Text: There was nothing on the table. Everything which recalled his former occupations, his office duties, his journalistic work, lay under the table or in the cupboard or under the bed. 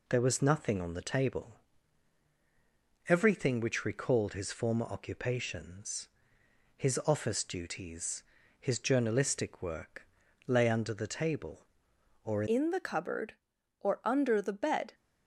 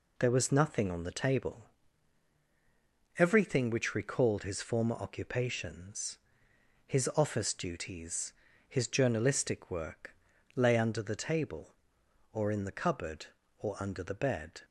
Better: second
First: changes voice at "in"; from 12.4 s on; 2.5 s long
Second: none

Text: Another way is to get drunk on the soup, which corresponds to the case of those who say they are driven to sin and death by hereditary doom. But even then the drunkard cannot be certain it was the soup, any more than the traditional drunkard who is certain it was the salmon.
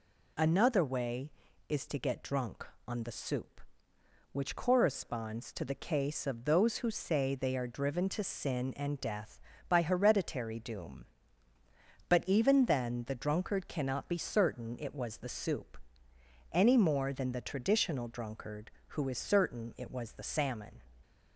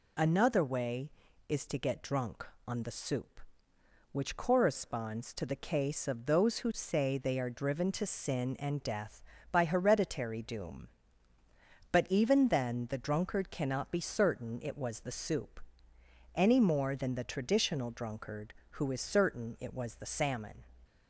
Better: neither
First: none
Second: none

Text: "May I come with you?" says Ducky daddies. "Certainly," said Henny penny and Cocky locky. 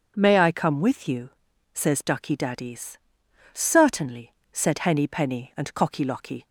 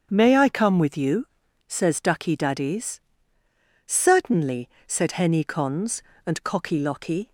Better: first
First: starts louder than the rest; until 1.1 s; 6.5 dB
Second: starts louder than the rest; strong; until 1.1 s; 7.5 dB // says "cons" for "penny"; at 5.4 s

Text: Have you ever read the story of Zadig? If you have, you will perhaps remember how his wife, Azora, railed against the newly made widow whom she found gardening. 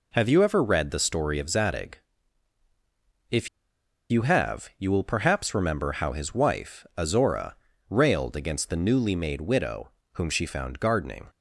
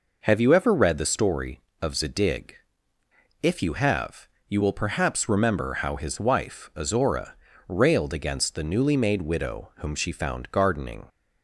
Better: second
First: pauses between "If" and "you"; noticeable; at 3.4 s; 0.62 s long // pauses between "widow" and "whom"; slight; at 9.9 s; 0.22 s long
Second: none

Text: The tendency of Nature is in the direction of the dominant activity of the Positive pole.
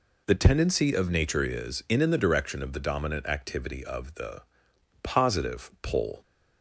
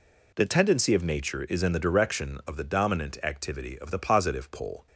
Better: second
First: says "in" twice; at 2.0 s // pauses between "the" and "Positive"; noticeable; at 4.4 s; 0.60 s long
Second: none

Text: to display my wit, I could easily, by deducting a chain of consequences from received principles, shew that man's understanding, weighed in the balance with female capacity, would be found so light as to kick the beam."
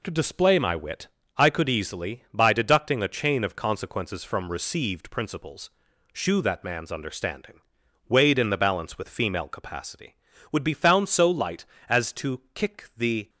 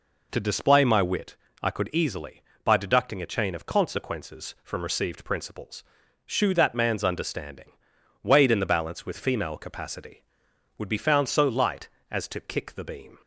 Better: second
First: stops before "beam"; at 13.2 s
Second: none

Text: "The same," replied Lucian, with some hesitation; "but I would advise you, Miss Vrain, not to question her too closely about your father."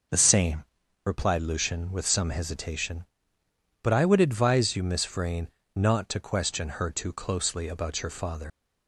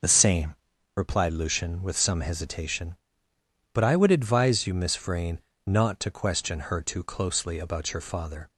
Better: second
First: leaves "father" unfinished; at 8.5 s; 90 ms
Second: none

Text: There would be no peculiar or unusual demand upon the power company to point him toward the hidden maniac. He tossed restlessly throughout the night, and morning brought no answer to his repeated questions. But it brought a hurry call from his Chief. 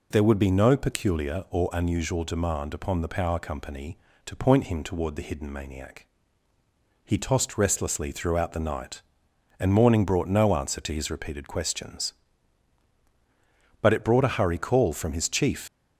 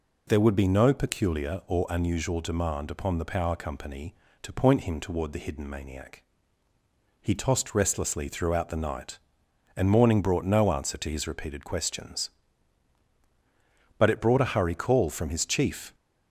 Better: second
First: leaves "Chief" unfinished; at 15.6 s; 95 ms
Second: none

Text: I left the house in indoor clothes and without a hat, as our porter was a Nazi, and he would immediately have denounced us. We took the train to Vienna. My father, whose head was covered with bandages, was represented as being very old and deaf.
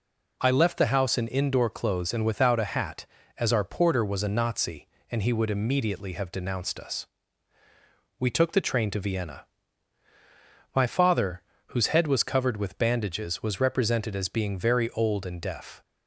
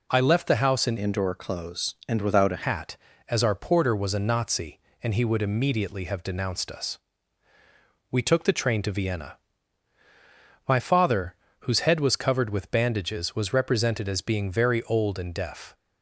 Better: first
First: none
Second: changes voice from "indoor" to "a"; from 0.9 to 2.6 s; 1.7 s long

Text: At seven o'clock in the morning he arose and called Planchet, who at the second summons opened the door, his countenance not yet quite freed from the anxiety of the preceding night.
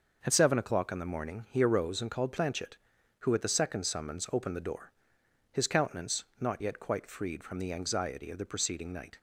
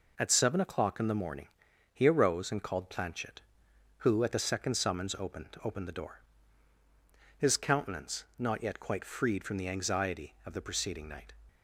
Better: first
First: pauses between "countenance" and "not"; slight; at 6.2 s; 0.16 s long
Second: pauses between "morning" and "he"; at 1.4 s; 0.44 s long // says "opened" twice; at 5.6 s // pauses between "countenance" and "not"; slight; at 8.2 s; 0.16 s long

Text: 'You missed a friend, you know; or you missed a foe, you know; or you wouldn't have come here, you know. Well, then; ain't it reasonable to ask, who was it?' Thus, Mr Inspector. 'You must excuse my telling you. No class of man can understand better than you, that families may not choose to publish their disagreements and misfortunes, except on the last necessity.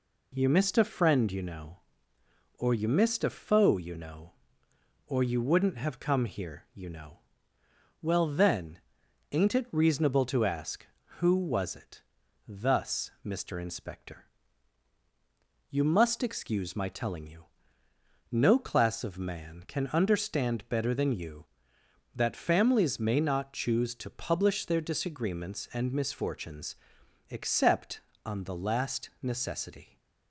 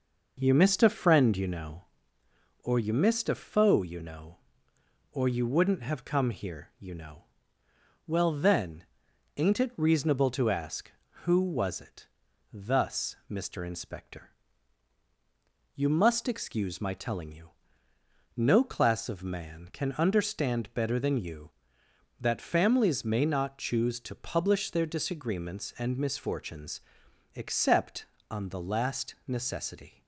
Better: first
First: none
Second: starts louder than the rest; noticeable; until 2.0 s; 5.5 dB

